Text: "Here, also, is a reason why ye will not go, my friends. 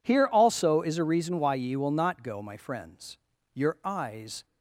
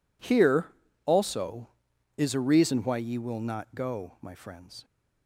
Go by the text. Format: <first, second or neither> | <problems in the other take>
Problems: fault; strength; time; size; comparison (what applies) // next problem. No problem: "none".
second | goes on to say "Your eyes"; noticeable; from 3.5 s on; 0.92 s long